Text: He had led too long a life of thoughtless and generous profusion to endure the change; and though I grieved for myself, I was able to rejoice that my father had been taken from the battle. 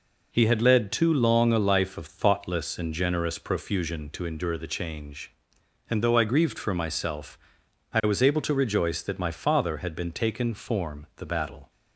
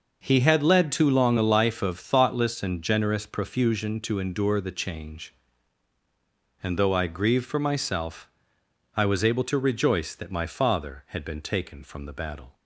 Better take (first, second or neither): second